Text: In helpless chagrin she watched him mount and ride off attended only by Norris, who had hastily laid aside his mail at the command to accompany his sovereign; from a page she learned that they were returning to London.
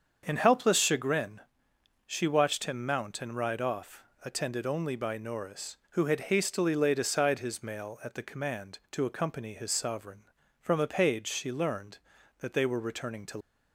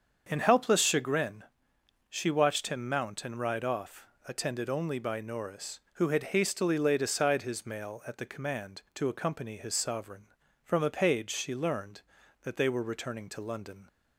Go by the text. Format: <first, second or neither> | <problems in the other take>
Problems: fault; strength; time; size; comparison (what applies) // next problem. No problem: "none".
second | starts louder than the rest; until 1.2 s; 7 dB; also in the second // pauses between "chagrin" and "she"; noticeable; at 1.4 s; 0.64 s long; noticeable in the second // pauses between "off" and "attended"; slight; at 4.0 s; 0.22 s long; slight in the second // stops before "London"; at 13.4 s